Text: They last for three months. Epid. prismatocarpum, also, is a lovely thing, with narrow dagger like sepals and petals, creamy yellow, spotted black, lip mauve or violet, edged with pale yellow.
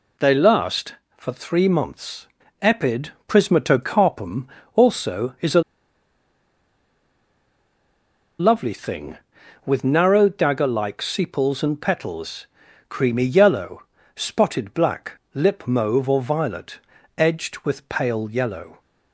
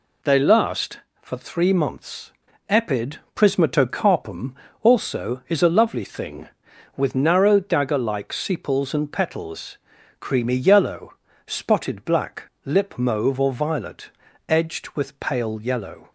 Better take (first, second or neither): second